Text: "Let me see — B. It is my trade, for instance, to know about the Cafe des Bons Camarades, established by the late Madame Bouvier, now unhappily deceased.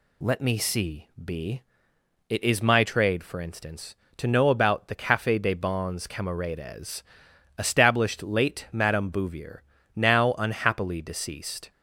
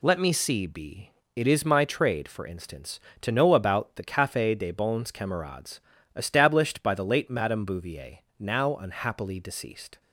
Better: second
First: skips "by the"; at 8.2 s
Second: none

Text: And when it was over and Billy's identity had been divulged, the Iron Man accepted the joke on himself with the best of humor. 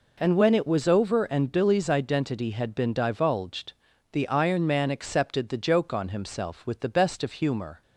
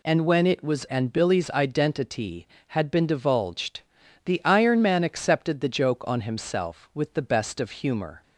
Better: first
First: none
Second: skips "over"; at 0.8 s

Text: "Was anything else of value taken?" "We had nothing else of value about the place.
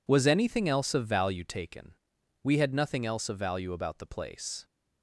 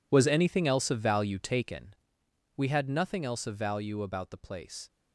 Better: first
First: none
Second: gets quieter; strong; throughout; 14.5 dB

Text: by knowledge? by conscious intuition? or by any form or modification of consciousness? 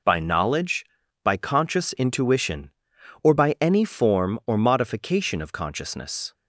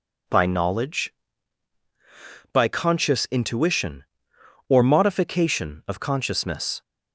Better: first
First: none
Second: skips "by any form or"; at 4.8 s

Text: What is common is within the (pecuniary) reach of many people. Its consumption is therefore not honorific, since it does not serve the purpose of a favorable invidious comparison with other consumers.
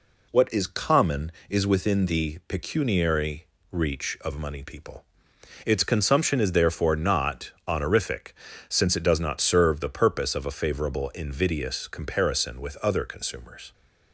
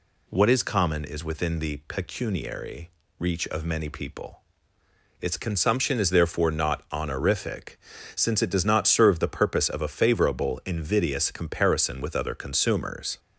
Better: second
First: says "money" for "many"; at 4.3 s // pauses between "not" and "honorific"; slight; at 7.5 s; 0.16 s long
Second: none

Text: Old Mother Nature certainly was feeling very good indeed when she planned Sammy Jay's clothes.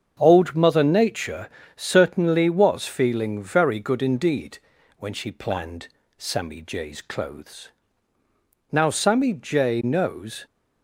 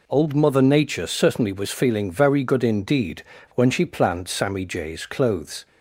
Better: second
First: starts louder than the rest; until 1.2 s; 7 dB // pauses between "Nature" and "certainly"; slight; at 1.4 s; 0.28 s long // pauses between "indeed" and "when"; at 4.5 s; 0.40 s long // pauses between "planned" and "Sammy"; slight; at 5.8 s; 0.32 s long // goes on to say "Now Sammy Jay knows"; strong; from 8.7 s on; 1.7 s long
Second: pauses between "indeed" and "when"; slight; at 3.2 s; 0.32 s long

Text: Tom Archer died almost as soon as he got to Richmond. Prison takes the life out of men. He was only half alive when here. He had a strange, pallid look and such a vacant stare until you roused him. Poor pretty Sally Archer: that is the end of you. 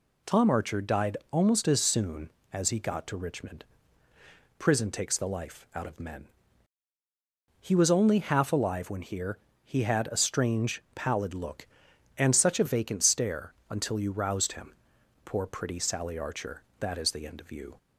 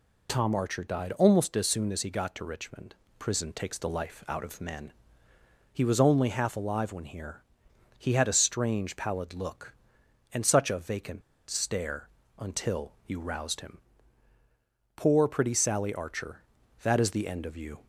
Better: first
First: pauses between "stare" and "until"; slight; at 13.5 s; 0.16 s long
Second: pauses between "vacant" and "stare"; slight; at 11.2 s; 0.27 s long // pauses between "stare" and "until"; slight; at 12.0 s; 0.30 s long

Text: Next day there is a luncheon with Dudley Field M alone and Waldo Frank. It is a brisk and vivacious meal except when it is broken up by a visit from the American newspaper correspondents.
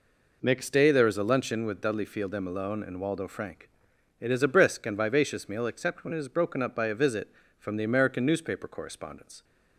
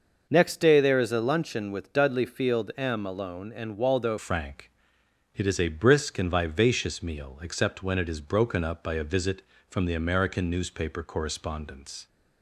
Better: first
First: none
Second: starts louder than the rest; noticeable; until 1.3 s; 6 dB // changes voice at "Frank"; from 4.1 s on; 7.9 s long

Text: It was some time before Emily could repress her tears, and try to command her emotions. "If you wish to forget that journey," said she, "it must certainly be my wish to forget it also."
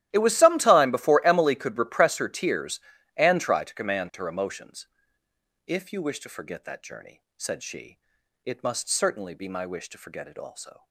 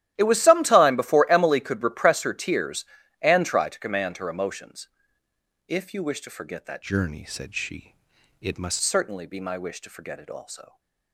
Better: first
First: starts louder than the rest; strong; until 1.1 s; 13 dB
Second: starts louder than the rest; strong; until 1.1 s; 13 dB // changes voice from "journey" to "must"; from 6.8 to 8.8 s; 2.0 s long

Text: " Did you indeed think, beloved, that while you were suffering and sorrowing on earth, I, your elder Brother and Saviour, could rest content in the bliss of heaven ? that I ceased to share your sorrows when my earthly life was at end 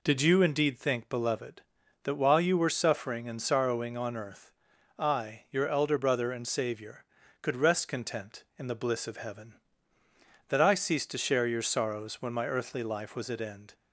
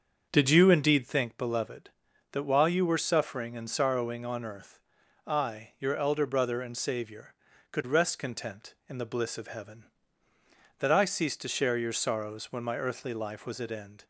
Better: first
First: none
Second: starts louder than the rest; until 1.3 s; 7 dB

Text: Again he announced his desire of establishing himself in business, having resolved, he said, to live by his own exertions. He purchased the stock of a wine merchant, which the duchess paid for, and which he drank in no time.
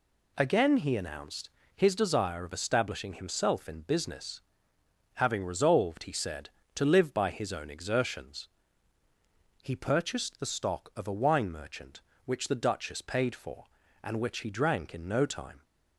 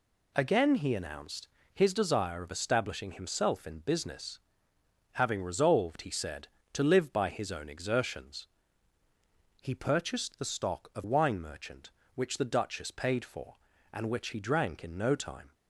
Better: first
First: pauses between "announced" and "his"; slight; at 1.4 s; 0.28 s long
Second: pauses between "announced" and "his"; slight; at 1.4 s; 0.28 s long // skips "a"; at 11.0 s

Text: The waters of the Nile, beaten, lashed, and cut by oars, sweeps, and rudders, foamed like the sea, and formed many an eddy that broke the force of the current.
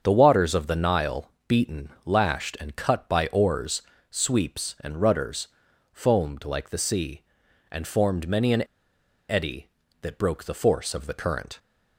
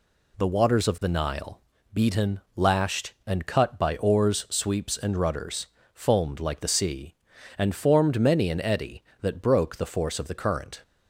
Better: second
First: starts louder than the rest; strong; until 1.0 s; 7.5 dB // pauses between "an" and "eddy"; noticeable; at 8.6 s; 0.63 s long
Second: none

